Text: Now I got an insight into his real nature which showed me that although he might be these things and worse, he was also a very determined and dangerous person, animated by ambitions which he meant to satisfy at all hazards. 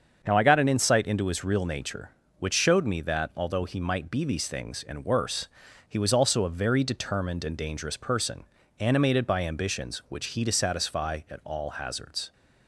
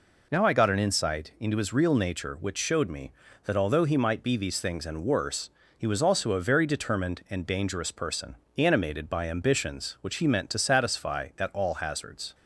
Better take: second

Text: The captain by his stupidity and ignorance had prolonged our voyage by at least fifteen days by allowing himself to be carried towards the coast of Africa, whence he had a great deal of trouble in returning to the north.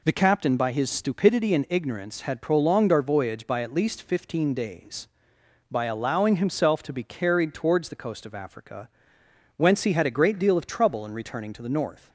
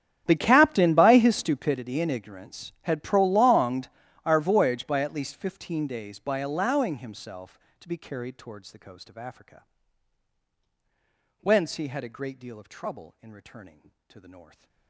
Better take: first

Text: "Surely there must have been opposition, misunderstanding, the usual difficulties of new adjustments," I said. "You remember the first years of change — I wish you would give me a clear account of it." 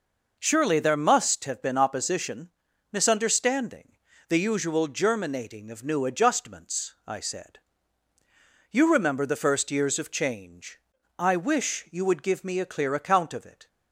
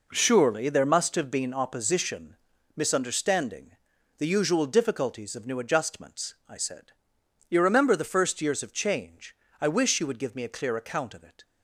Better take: second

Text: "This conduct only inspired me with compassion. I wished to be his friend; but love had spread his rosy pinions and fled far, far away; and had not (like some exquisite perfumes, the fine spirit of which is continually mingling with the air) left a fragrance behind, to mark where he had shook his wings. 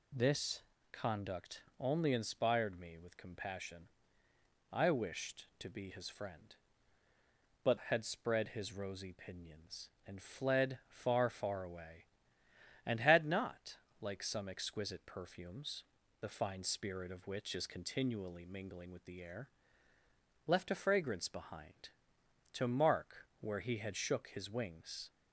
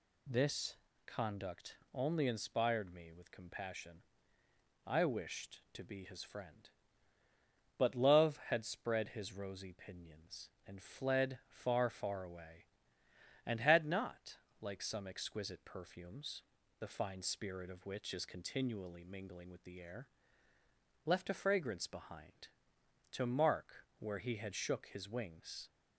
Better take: second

